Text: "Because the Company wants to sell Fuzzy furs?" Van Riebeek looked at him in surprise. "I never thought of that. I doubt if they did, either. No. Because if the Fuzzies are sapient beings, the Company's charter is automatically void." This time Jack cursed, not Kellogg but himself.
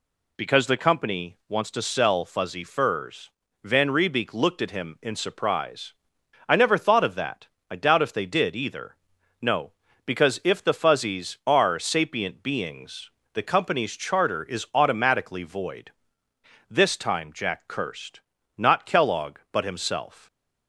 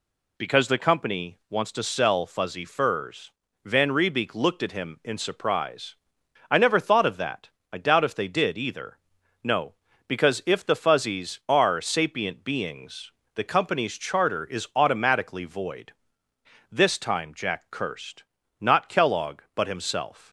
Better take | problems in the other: neither | none

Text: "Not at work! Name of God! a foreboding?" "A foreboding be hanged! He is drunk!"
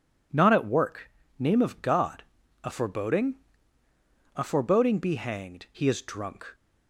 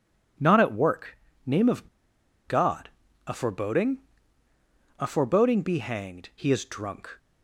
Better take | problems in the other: first | pauses between "of" and "God"; noticeable; at 1.8 s; 0.59 s long

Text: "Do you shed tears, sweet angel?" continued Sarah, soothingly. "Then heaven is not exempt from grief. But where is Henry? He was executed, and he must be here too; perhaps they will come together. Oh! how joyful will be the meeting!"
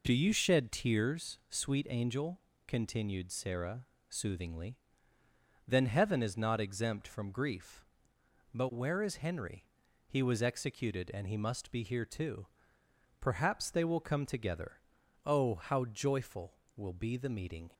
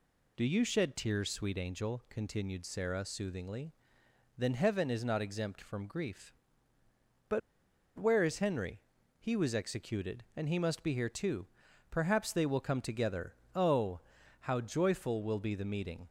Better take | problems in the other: first | pauses between "But" and "where"; noticeable; at 7.4 s; 0.58 s long

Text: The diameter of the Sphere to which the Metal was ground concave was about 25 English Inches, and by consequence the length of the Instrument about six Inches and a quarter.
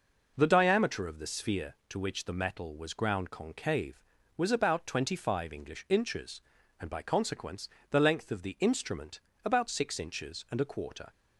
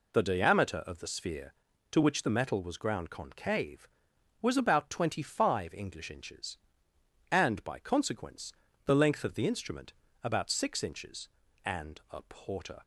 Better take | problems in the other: first | pauses between "consequence" and "the"; slight; at 8.5 s; 0.34 s long; slight in the first // pauses between "Instrument" and "about"; slight; at 9.9 s; 0.32 s long; slight in the first // says "porter" for "quarter"; at 12.2 s

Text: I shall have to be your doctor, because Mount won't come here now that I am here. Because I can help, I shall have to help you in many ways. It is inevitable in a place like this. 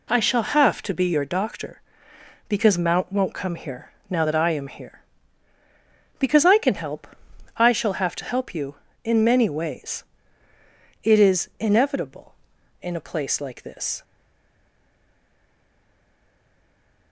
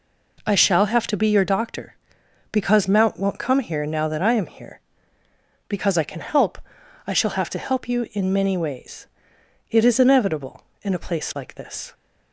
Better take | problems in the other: second | pauses between "here" and "now"; slight; at 3.9 s; 0.18 s long // stays silent after the last word; strong; from 14.0 s on; 3.1 s long

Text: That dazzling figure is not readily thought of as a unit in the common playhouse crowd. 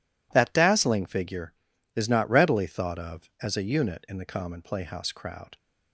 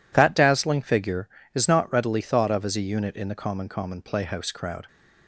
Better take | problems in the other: first | says "common" twice; at 3.6 s

